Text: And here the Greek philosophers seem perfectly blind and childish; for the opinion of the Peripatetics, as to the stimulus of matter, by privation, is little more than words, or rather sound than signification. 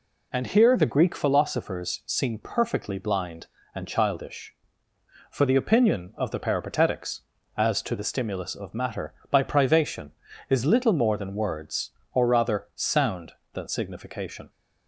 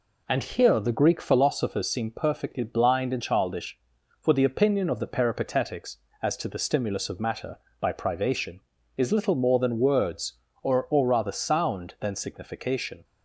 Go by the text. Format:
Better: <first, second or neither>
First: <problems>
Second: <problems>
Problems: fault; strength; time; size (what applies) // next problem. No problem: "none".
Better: first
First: none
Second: says "or" twice; at 10.9 s